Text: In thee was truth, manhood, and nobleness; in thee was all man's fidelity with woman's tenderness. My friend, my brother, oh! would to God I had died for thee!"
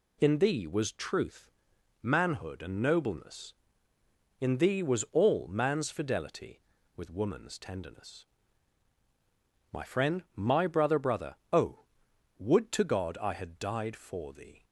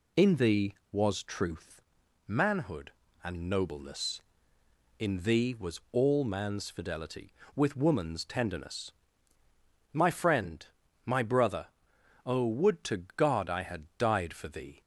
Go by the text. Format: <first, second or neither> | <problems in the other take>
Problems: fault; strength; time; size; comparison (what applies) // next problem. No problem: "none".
second | says "brother" twice; at 10.9 s